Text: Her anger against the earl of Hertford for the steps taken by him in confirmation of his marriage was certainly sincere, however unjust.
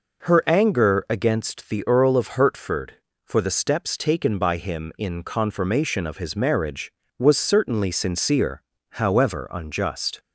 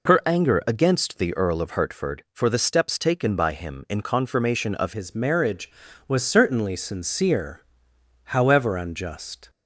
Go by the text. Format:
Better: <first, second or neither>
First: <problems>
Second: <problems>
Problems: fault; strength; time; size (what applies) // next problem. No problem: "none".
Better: first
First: none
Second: changes voice at "his"; from 4.9 s on; 4.5 s long